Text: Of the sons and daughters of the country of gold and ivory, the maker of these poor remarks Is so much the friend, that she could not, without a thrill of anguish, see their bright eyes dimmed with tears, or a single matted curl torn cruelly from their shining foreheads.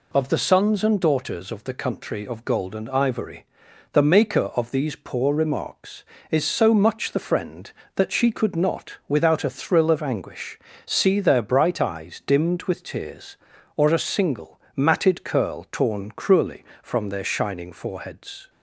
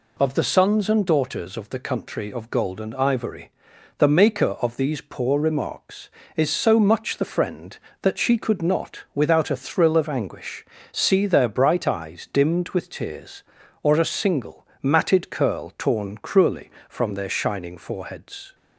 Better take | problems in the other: neither | pauses between "single" and "matted"; slight; the same in both

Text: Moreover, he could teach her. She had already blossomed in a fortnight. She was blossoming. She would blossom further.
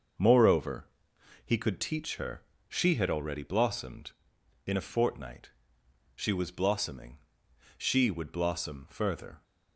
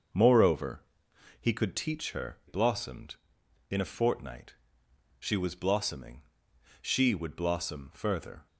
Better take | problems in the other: first | starts louder than the rest; until 1.7 s; 6 dB; noticeable in the first // skips "She had already"; at 2.4 s

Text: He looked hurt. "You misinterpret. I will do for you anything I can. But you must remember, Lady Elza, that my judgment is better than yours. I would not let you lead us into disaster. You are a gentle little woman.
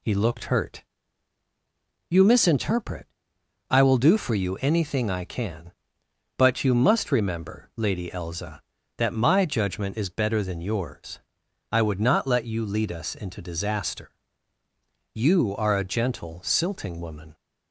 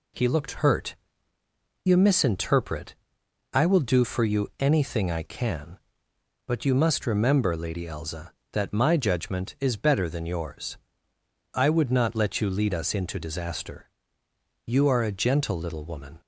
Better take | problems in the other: second | says "silting" for "little"; at 16.4 s

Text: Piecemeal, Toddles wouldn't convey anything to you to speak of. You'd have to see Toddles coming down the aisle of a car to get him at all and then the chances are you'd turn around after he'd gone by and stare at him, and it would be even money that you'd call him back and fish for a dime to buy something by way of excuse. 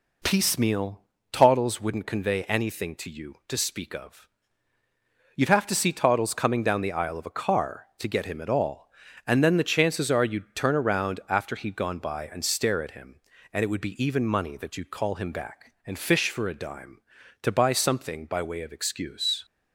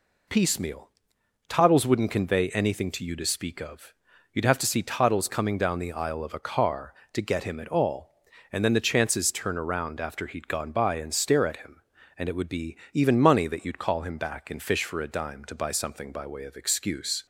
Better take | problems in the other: first | skips "are you'd"; at 9.3 s // pauses between "be" and "even"; slight; at 12.7 s; 0.16 s long

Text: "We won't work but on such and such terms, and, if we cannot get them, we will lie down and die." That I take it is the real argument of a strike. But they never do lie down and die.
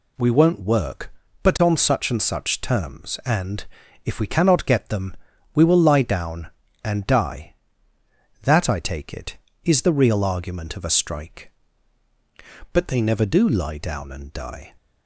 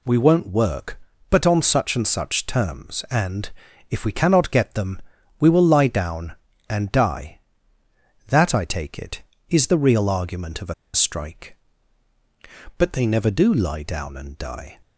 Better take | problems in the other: first | pauses between "a" and "strike"; slight; at 10.7 s; 0.20 s long

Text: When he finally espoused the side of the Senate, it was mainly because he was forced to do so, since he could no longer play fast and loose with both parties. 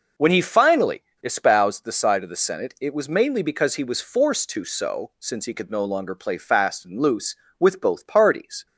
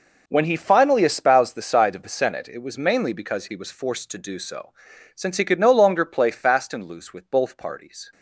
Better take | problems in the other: second | pauses between "finally" and "espoused"; slight; at 1.0 s; 0.20 s long // skips "do"; at 4.6 s

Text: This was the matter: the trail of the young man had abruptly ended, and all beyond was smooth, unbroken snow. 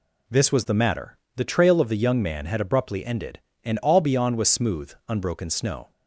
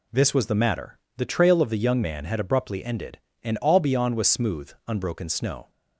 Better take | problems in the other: neither | none

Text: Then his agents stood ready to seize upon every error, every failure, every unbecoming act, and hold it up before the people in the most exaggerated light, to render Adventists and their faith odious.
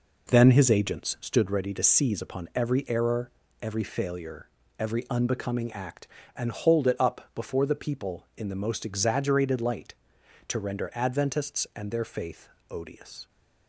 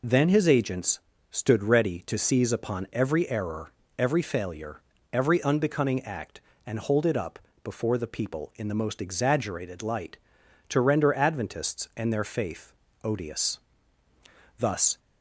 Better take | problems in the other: first | pauses between "agents" and "stood"; slight; at 0.9 s; 0.32 s long // pauses between "up" and "before"; slight; at 7.3 s; 0.24 s long // pauses between "faith" and "odious"; slight; at 12.7 s; 0.28 s long; slight in the first // goes on to say "Thus"; slight; from 14.5 s on; 0.40 s long

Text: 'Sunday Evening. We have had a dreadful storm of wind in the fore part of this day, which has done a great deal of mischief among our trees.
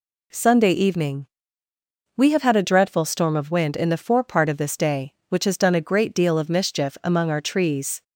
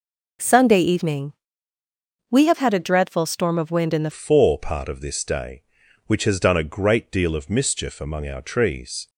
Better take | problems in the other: first | changes voice at "fore"; from 4.1 s on; 4.9 s long

